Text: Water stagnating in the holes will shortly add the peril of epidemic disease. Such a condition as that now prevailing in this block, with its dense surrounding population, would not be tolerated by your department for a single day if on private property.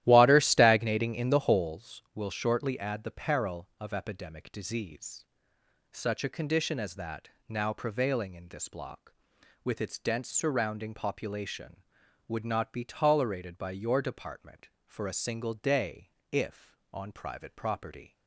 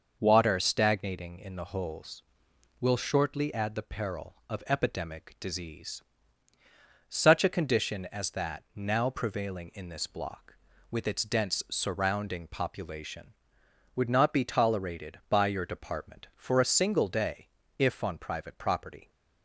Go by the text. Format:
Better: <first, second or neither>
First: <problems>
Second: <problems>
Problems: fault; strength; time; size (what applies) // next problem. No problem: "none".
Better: second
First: starts louder than the rest; strong; until 1.7 s; 13.5 dB // pauses between "that" and "now"; slight; at 7.2 s; 0.18 s long // pauses between "day" and "if"; slight; at 16.0 s; 0.24 s long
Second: pauses between "day" and "if"; slight; at 17.4 s; 0.28 s long